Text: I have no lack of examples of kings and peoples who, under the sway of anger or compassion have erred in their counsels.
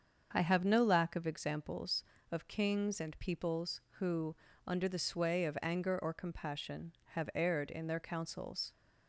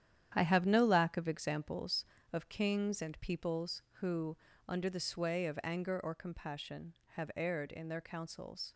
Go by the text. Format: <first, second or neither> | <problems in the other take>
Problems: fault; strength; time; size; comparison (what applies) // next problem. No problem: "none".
first | gets quieter; strong; throughout; 8.5 dB // starts louder than the rest; strong; until 1.3 s; 10 dB; also in the first